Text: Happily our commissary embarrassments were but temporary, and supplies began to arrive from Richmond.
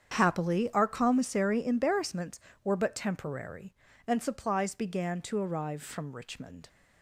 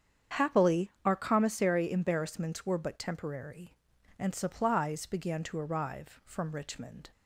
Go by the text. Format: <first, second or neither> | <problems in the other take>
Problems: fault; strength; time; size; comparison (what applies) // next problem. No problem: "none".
neither | starts louder than the rest; strong; the same in both